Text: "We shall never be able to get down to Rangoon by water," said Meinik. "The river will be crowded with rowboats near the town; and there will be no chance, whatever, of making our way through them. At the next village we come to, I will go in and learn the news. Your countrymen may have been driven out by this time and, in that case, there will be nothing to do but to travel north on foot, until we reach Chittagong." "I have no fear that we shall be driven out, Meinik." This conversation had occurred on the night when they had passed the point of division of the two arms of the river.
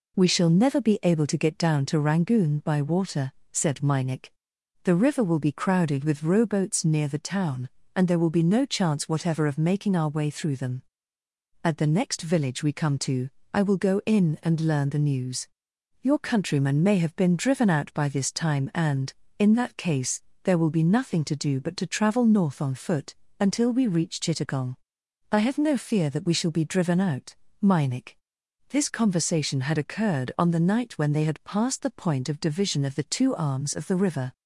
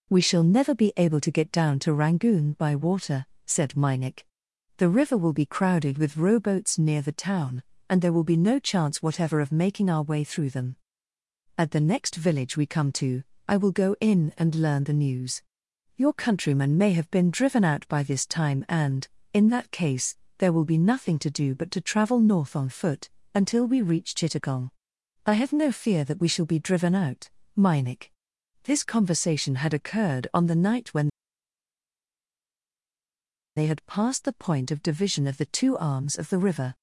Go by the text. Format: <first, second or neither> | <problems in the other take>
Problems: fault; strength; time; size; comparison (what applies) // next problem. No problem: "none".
first | pauses between "when" and "they"; strong; at 31.0 s; 2.4 s long